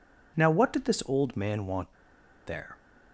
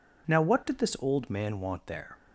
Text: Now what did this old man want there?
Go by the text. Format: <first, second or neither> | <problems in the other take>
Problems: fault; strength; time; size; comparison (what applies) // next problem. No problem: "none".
second | pauses between "want" and "there"; noticeable; at 1.9 s; 0.55 s long